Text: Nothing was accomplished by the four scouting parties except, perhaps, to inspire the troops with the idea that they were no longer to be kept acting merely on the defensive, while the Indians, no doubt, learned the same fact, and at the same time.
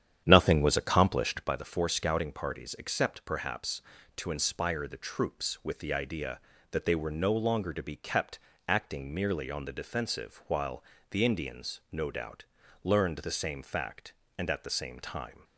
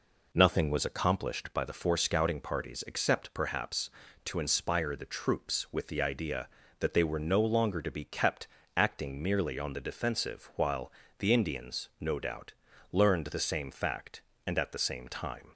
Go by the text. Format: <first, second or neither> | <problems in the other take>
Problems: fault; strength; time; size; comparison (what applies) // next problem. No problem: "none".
second | starts louder than the rest; strong; until 1.6 s; 9.5 dB // pauses between "kept" and "acting"; slight; at 8.3 s; 0.30 s long; slight in the second // pauses between "while" and "the"; slight; at 10.8 s; 0.26 s long; slight in the second